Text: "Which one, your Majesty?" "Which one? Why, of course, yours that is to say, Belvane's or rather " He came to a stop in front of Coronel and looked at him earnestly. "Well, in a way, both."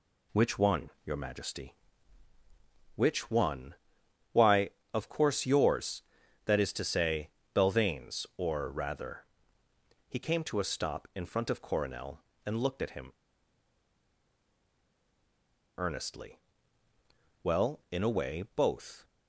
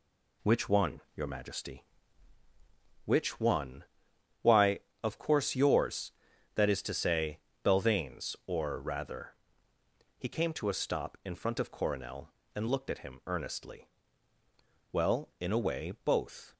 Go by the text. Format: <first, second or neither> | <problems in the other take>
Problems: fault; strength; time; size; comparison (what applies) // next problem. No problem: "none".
second | pauses between "him" and "earnestly"; strong; at 13.1 s; 2.6 s long